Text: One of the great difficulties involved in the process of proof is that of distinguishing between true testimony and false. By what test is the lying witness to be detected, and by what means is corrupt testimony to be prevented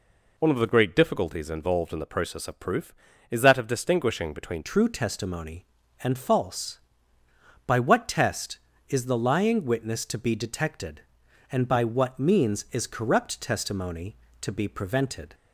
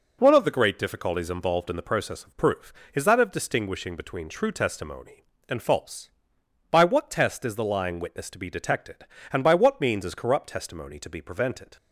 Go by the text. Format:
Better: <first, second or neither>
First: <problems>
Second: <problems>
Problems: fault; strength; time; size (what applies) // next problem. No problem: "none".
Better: second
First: changes voice at "true"; from 4.6 s on; 10.7 s long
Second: none